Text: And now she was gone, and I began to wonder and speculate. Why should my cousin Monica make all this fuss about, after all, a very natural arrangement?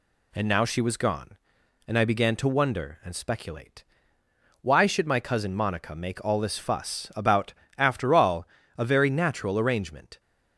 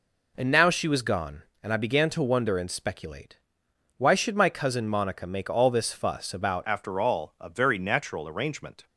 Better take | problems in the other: first | changes voice at "after"; from 6.6 s on; 2.2 s long

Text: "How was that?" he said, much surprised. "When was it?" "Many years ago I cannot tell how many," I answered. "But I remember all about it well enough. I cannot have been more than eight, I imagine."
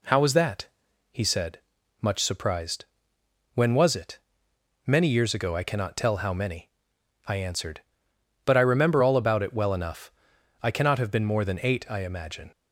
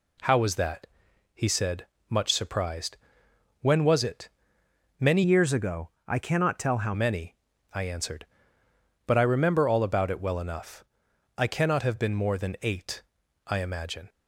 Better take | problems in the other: first | changes voice from "years" to "how"; from 5.2 to 6.9 s; 1.7 s long // pauses between "ago" and "I"; slight; at 5.9 s; 0.18 s long

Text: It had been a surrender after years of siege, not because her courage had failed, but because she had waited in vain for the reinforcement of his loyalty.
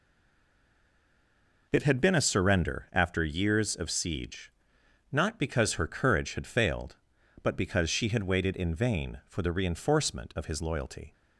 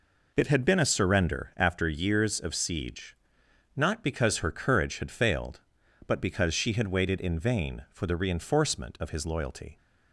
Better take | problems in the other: second | stays silent before the first word; noticeable; until 1.7 s; 1.7 s long

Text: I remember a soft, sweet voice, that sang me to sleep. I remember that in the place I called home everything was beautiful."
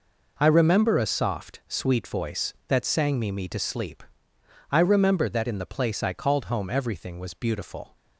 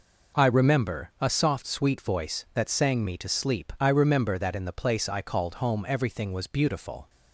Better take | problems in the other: second | says "me" twice; at 3.3 s

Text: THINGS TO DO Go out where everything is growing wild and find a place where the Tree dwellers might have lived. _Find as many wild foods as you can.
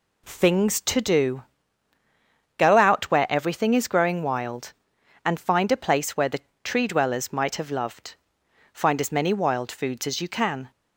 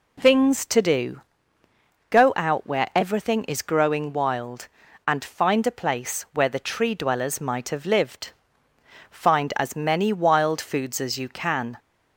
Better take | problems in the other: second | pauses between "DO" and "Go"; at 1.4 s; 1.1 s long; noticeable in the second // pauses between "the" and "Tree"; slight; at 6.4 s; 0.22 s long // says "loved" for "lived"; at 7.7 s

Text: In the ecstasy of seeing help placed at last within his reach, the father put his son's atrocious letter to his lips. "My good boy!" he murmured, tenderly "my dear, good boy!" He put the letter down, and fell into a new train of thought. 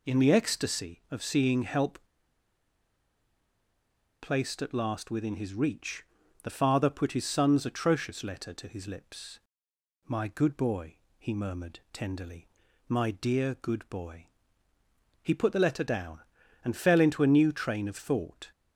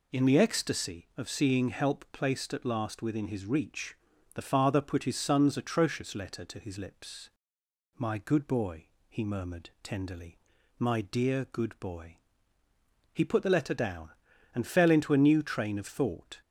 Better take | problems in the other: second | pauses between "help" and "placed"; strong; at 1.9 s; 2.2 s long // pauses between "tenderly" and "my"; at 12.4 s; 0.40 s long; also in the second

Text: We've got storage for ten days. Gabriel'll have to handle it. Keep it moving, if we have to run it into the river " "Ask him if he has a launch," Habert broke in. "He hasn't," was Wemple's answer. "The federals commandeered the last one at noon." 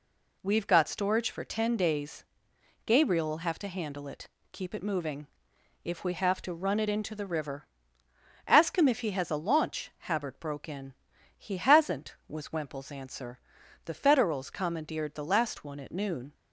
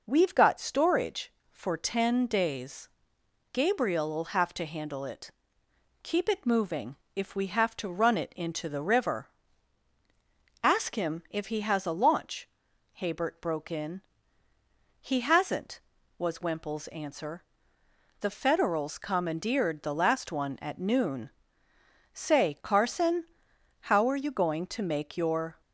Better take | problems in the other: first | starts louder than the rest; noticeable; until 1.0 s; 6 dB // goes on to say "Say Carson how are you going to make your"; strong; from 22.1 s on; 3.4 s long

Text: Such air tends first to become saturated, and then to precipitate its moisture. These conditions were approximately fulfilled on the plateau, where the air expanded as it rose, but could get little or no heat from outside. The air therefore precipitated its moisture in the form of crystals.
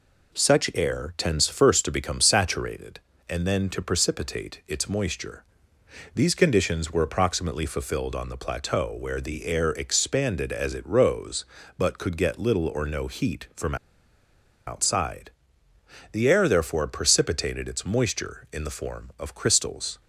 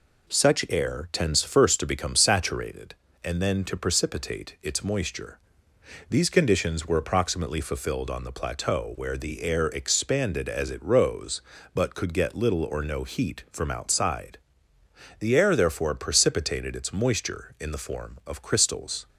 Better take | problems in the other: second | pauses between "from" and "outside"; noticeable; at 13.7 s; 0.91 s long

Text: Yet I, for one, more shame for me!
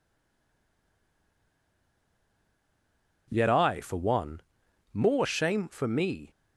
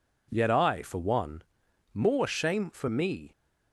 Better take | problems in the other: second | stays silent before the first word; strong; until 3.2 s; 3.2 s long

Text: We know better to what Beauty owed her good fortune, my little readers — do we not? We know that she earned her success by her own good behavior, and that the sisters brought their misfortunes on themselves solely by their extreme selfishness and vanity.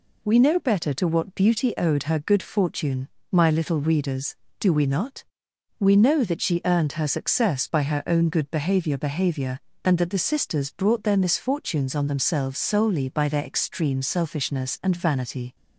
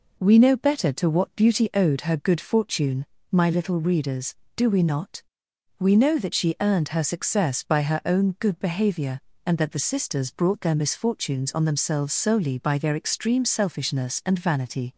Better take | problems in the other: second | says "behavior" twice; at 8.9 s

